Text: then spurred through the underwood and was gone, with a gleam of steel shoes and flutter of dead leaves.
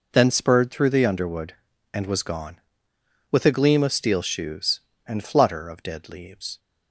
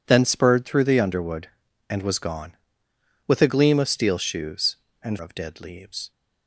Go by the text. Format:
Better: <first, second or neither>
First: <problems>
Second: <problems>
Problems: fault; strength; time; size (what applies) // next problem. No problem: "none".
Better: first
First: none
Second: skips "flutter"; at 5.1 s